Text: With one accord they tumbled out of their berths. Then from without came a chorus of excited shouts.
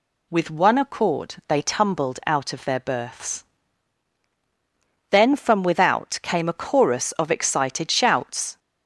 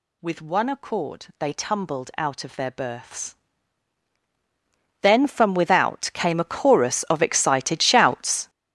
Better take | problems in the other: first | gets louder; strong; throughout; 11 dB

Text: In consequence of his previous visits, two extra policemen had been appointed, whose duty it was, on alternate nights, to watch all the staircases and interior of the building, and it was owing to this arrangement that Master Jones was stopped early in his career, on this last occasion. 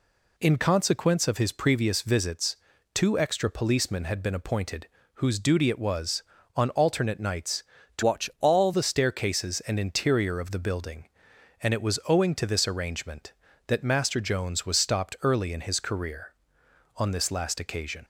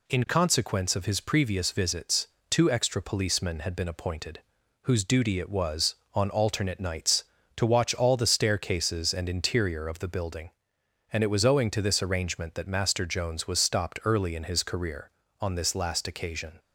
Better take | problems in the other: second | changes voice from "watch" to "all"; from 8.0 to 8.7 s; 0.7 s long

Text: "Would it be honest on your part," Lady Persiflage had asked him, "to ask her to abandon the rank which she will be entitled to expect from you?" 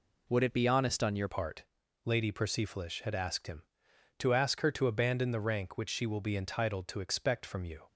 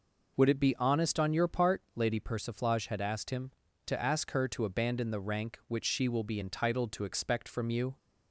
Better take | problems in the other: second | changes voice at "part"; from 1.2 s on; 6.6 s long

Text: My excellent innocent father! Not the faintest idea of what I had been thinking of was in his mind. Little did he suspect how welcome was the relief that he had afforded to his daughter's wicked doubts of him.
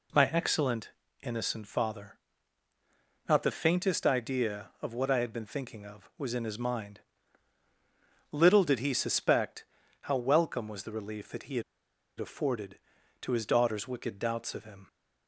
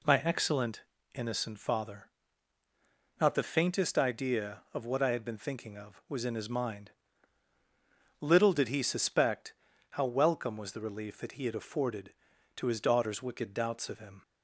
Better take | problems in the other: second | pauses between "excellent" and "innocent"; slight; at 0.9 s; 0.32 s long; slight in the second // pauses between "suspect" and "how"; at 9.6 s; 0.38 s long; also in the second // pauses between "had" and "afforded"; noticeable; at 11.6 s; 0.56 s long

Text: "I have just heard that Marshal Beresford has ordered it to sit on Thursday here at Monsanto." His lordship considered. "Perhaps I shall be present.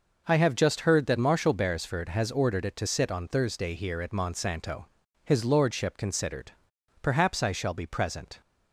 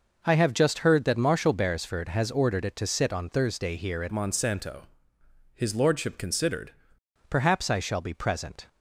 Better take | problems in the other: first | changes voice from "Monsanto" to "considered"; from 4.0 to 6.7 s; 2.7 s long

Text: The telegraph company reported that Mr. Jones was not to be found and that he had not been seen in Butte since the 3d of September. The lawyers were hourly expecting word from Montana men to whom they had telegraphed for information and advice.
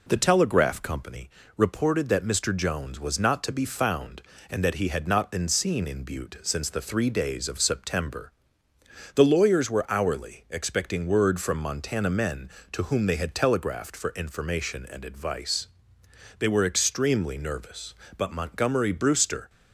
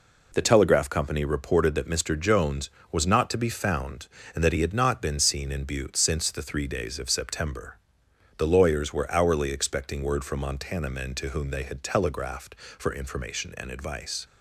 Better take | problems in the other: second | pauses between "company" and "reported"; slight; at 1.2 s; 0.28 s long // goes on to say "They were extremely nervous but Montgomery Brewster"; strong; from 16.3 s on; 3.1 s long

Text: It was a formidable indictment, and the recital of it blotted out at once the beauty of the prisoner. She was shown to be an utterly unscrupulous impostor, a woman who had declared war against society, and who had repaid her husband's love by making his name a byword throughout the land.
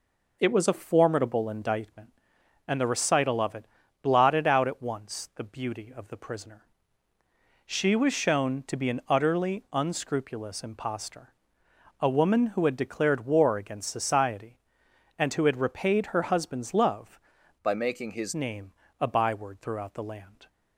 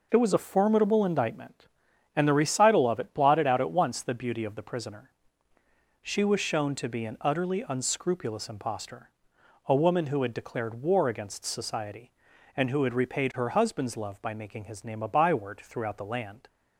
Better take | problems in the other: second | pauses between "it" and "blotted"; at 3.6 s; 0.38 s long // changes voice from "by" to "his"; from 17.6 to 18.3 s; 0.7 s long // pauses between "name" and "a"; slight; at 18.7 s; 0.28 s long

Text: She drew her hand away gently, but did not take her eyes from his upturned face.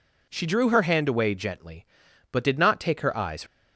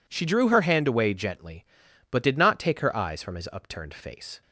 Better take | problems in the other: second | stops before "from his upturned face"; at 3.4 s

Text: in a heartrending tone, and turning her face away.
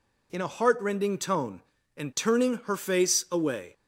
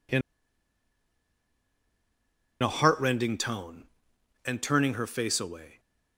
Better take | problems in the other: first | pauses between "in" and "a"; strong; at 0.2 s; 2.4 s long

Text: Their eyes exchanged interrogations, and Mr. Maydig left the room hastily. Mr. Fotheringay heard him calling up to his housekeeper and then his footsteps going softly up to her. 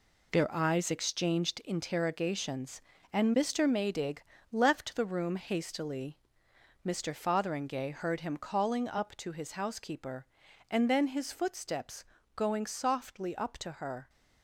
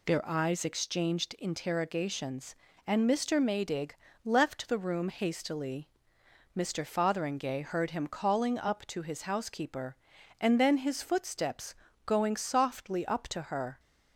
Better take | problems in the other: second | gets quieter; strong; throughout; 7.5 dB // pauses between "Maydig" and "left"; slight; at 4.2 s; 0.32 s long; slight in the second // pauses between "footsteps" and "going"; slight; at 12.0 s; 0.32 s long; slight in the second

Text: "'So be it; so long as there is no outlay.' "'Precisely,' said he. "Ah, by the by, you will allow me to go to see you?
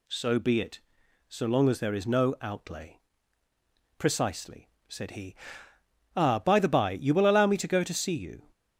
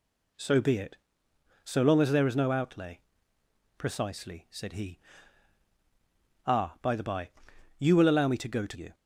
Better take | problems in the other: first | skips "see"; at 8.7 s

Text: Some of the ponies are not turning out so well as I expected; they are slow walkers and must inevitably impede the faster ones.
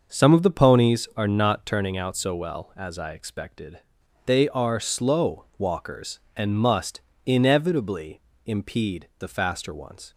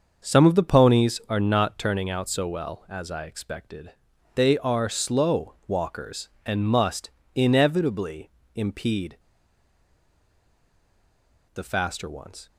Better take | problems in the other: first | starts louder than the rest; until 1.3 s; 6 dB; also in the first // pauses between "must" and "inevitably"; slight; at 7.0 s; 0.24 s long; slight in the first // pauses between "inevitably" and "impede"; slight; at 8.2 s; 0.24 s long; slight in the first // pauses between "impede" and "the"; strong; at 9.1 s; 2.3 s long

